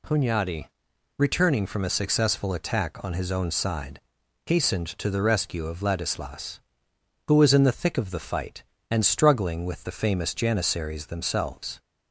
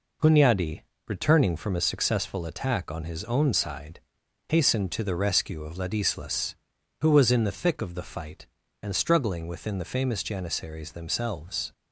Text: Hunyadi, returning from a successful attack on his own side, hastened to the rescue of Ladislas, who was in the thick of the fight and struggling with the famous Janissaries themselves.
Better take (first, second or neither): first